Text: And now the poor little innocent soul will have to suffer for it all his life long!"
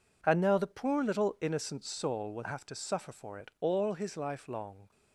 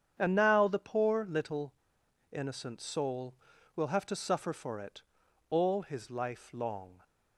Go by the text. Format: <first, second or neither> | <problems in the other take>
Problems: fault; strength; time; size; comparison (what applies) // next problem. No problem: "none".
first | starts louder than the rest; strong; until 1.2 s; 8 dB // pauses between "little" and "innocent"; noticeable; at 1.7 s; 0.58 s long // pauses between "it" and "all"; noticeable; at 5.0 s; 0.48 s long